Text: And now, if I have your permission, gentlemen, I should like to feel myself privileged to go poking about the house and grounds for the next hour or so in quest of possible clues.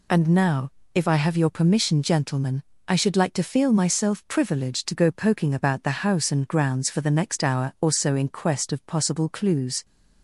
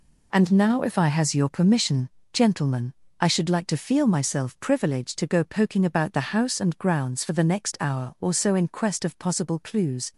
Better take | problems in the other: first | says "has" for "have"; at 1.0 s

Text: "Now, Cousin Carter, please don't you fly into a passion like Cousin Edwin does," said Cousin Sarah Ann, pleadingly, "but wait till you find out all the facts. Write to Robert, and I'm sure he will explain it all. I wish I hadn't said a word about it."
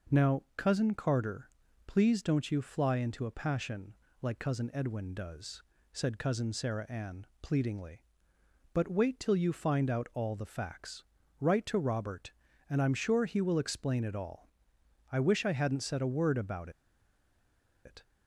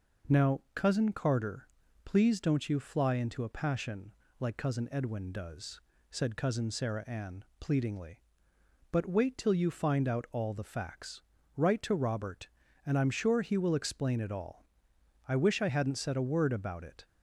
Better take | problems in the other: second | pauses between "passion" and "like"; slight; at 3.9 s; 0.28 s long; slight in the second // pauses between "about" and "it"; at 16.6 s; 1.1 s long

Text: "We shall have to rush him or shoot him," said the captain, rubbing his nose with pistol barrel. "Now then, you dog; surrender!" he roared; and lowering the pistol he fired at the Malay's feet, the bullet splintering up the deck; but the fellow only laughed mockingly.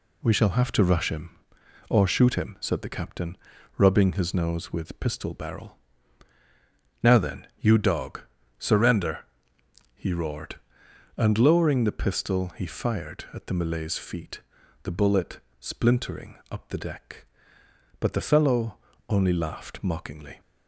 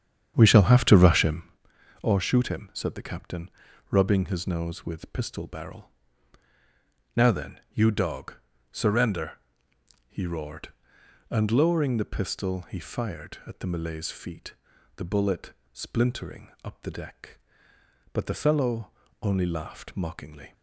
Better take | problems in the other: first | starts louder than the rest; strong; until 1.6 s; 8.5 dB // pauses between "bullet" and "splintering"; slight; at 15.5 s; 0.18 s long; slight in the first // pauses between "fellow" and "only"; slight; at 18.9 s; 0.30 s long; slight in the first

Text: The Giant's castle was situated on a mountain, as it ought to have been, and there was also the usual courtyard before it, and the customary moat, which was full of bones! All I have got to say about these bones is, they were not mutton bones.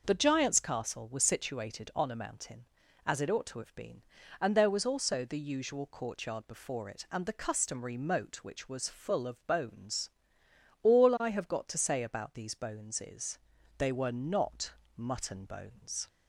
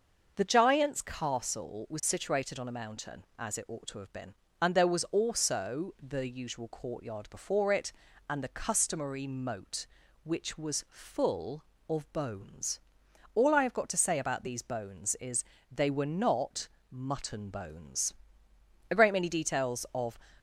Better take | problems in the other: first | starts louder than the rest; until 1.3 s; 6.5 dB; noticeable in the first // pauses between "not" and "mutton"; slight; at 16.6 s; 0.22 s long; slight in the first // goes on to say "A great many details of"; noticeable; from 18.8 s on; 1.2 s long

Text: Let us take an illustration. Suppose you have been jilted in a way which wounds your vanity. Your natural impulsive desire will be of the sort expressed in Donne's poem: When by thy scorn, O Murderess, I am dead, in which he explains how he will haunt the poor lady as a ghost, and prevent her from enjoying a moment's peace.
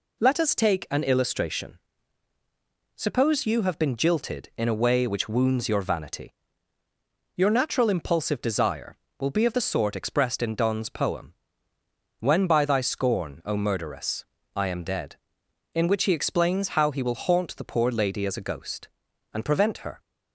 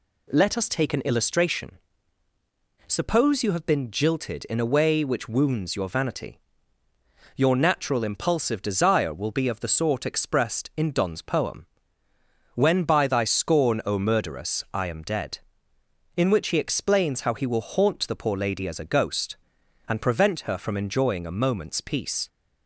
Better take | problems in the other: second | stops before "from enjoying a moment's peace"; at 20.0 s

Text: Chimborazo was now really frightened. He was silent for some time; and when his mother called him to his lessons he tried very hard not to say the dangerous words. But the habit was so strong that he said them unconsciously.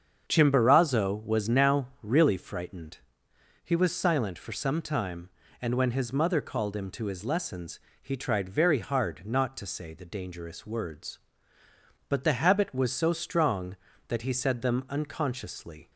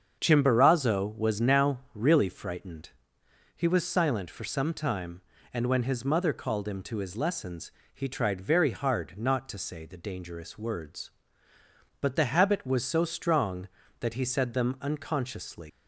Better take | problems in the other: first | starts louder than the rest; strong; until 1.2 s; 7 dB; strong in the first // pauses between "lessons" and "he"; slight; at 7.7 s; 0.22 s long; slight in the first // leaves "unconsciously" unfinished; at 15.6 s; 125 ms

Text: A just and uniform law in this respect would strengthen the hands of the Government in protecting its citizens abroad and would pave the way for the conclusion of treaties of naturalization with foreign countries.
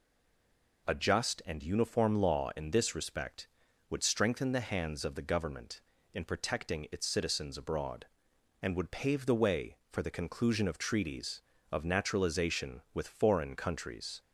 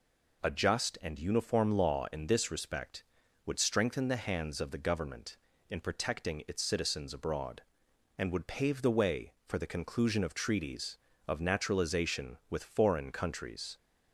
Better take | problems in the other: second | stays silent before the first word; slight; until 0.8 s; 0.8 s long

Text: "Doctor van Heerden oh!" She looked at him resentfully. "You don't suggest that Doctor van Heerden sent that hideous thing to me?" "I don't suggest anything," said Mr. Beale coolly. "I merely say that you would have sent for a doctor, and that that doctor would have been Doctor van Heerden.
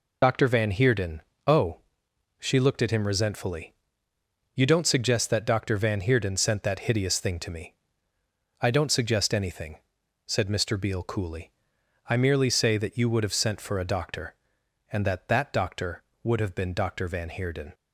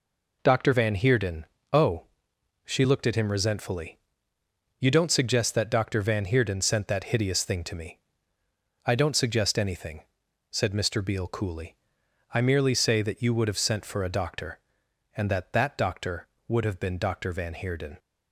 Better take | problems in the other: second | loses the start of "Doctor"; at 0.2 s; 70 ms // pauses between "Heerden" and "oh"; slight; at 1.2 s; 0.24 s long; slight in the second

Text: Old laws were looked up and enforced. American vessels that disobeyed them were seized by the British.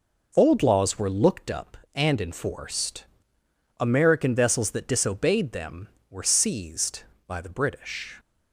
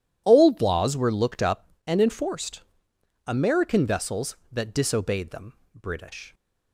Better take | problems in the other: first | skips "were seized by the"; at 5.6 s

